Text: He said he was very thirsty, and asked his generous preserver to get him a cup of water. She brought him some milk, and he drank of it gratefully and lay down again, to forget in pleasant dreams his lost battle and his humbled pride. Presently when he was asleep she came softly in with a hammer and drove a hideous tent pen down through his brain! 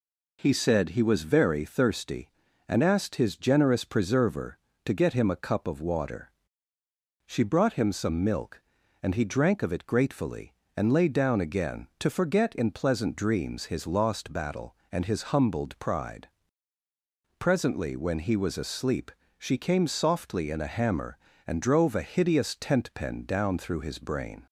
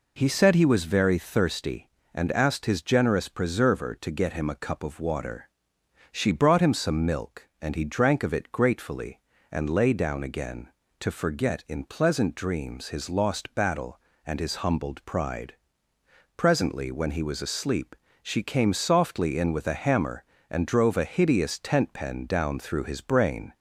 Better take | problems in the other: second | pauses between "asleep" and "she"; slight; at 19.1 s; 0.26 s long; slight in the second // skips "with"; at 20.6 s

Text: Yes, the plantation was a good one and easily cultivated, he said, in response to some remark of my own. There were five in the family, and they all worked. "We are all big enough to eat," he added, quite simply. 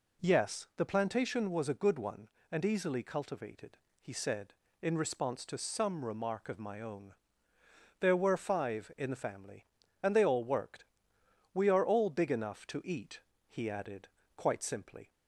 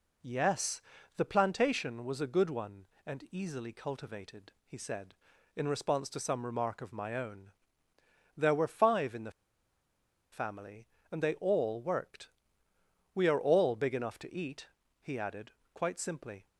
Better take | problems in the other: first | pauses between "the" and "family"; at 9.3 s; 1.0 s long

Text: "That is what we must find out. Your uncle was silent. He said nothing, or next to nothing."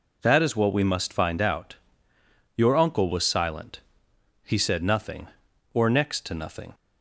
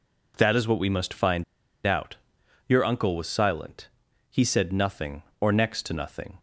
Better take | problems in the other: first | pauses between "find" and "out"; at 1.4 s; 0.42 s long

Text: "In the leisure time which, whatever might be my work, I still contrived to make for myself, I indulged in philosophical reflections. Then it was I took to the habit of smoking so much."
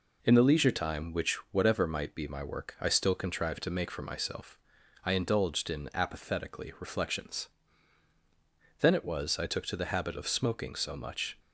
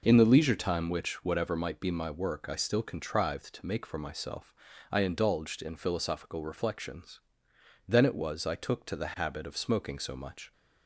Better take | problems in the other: second | says "apathetically" for "philosophical"; at 5.9 s

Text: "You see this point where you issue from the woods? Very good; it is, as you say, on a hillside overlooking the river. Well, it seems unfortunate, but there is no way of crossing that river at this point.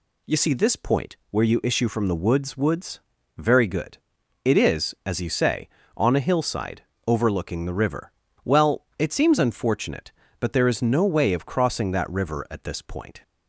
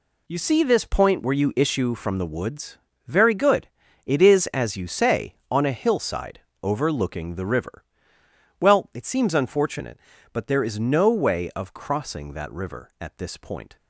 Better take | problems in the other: second | says "woods" twice; at 2.5 s // pauses between "hillside" and "overlooking"; slight; at 6.8 s; 0.24 s long; slight in the second

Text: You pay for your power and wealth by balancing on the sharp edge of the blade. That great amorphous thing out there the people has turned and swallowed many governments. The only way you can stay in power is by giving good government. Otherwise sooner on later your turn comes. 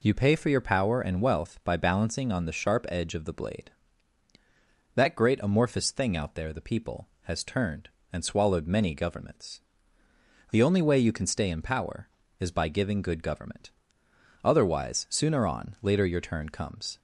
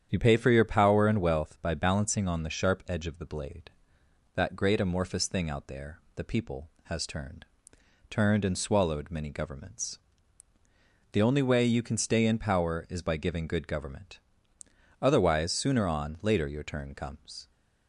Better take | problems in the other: first | starts louder than the rest; strong; until 1.1 s; 9 dB // pauses between "there" and "the"; slight; at 6.0 s; 0.16 s long // says "turned" twice; at 8.1 s

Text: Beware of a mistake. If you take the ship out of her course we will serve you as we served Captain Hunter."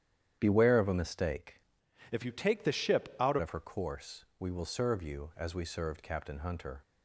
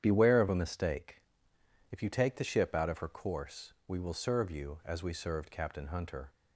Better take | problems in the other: second | starts louder than the rest; strong; until 1.4 s; 10 dB; strong in the second // changes voice from "If" to "out"; from 2.1 to 3.3 s; 1.2 s long

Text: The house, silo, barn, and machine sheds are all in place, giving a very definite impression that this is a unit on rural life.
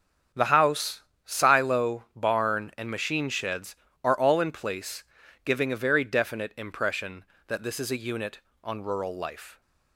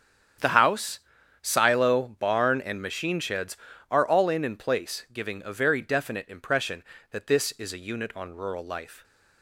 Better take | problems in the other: first | starts louder than the rest; strong; until 1.8 s; 8 dB; strong in the first // says "in" twice; at 4.4 s

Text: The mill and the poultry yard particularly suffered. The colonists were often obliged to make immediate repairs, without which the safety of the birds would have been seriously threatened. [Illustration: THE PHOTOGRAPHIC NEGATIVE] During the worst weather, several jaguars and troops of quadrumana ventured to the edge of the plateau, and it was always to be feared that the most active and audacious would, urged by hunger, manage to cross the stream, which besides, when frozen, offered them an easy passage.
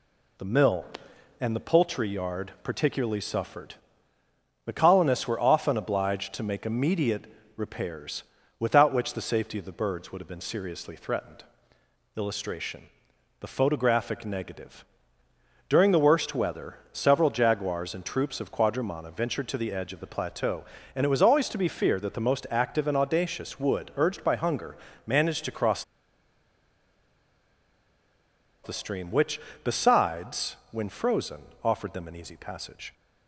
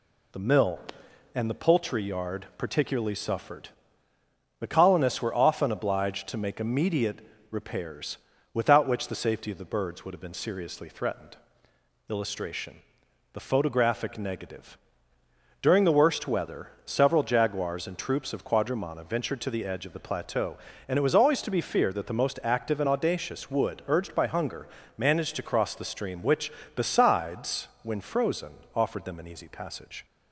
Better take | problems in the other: second | pauses between "immediate" and "repairs"; slight; at 7.2 s; 0.32 s long; slight in the second // pauses between "NEGATIVE" and "During"; noticeable; at 14.8 s; 0.84 s long; noticeable in the second // pauses between "cross" and "the"; strong; at 25.8 s; 2.8 s long // pauses between "which" and "besides"; slight; at 29.3 s; 0.24 s long; slight in the second

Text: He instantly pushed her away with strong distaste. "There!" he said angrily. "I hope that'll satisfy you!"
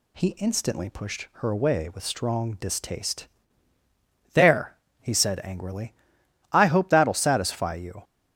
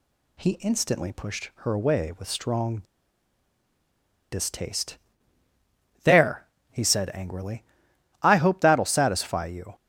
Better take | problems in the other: first | pauses between "strong" and "distaste"; strong; at 2.7 s; 1.5 s long

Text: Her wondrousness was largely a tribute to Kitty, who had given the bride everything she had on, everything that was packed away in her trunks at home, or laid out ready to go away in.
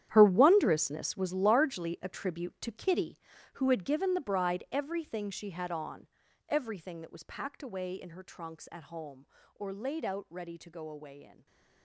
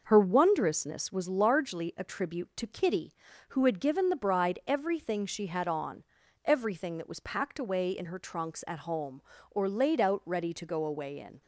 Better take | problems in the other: second | gets quieter; strong; throughout; 15 dB // stays silent after the last word; slight; from 11.3 s on; 0.5 s long

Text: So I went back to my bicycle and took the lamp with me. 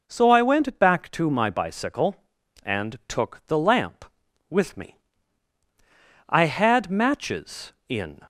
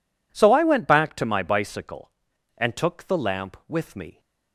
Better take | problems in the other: second | goes on to say "I had matches in"; strong; from 6.2 s on; 1.9 s long

